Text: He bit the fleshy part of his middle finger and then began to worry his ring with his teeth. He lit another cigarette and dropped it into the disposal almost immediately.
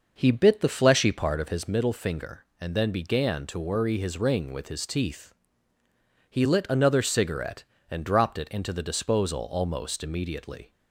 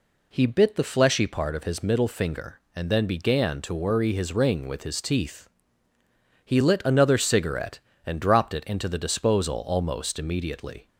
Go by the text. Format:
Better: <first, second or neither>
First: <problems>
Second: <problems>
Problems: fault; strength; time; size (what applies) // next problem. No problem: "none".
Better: second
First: starts louder than the rest; noticeable; until 1.7 s; 6 dB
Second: none